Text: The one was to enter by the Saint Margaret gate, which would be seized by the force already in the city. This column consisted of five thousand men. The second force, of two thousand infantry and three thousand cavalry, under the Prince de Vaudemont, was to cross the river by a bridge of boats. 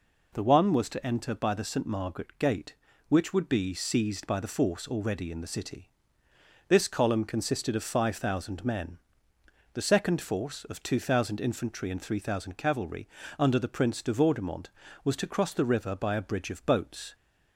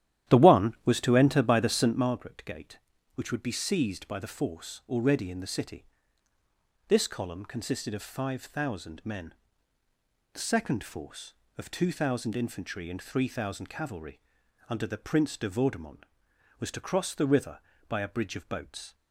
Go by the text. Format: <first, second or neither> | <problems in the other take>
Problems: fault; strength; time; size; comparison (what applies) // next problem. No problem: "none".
first | starts louder than the rest; strong; until 2.1 s; 12 dB